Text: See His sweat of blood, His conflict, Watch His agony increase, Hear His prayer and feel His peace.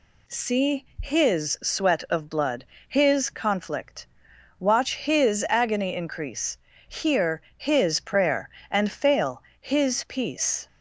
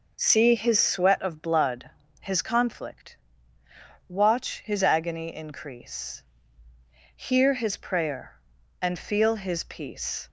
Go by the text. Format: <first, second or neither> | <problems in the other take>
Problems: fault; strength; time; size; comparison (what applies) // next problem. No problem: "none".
second | pauses between "See" and "His"; slight; at 0.8 s; 0.16 s long // pauses between "Hear" and "His"; slight; at 7.4 s; 0.16 s long // says "fail" for "feel"; at 8.9 s